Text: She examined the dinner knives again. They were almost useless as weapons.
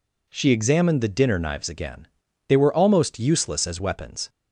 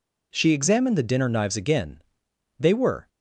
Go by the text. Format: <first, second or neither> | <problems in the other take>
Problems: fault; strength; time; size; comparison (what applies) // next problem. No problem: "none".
first | stops before "almost useless as weapons"; at 3.0 s